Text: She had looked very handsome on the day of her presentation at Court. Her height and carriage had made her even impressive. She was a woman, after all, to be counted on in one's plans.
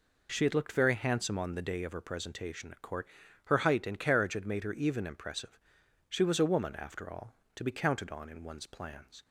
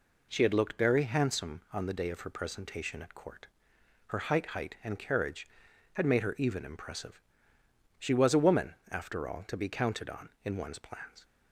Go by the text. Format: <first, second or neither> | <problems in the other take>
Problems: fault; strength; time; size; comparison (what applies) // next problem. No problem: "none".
first | says "height" twice; at 4.4 s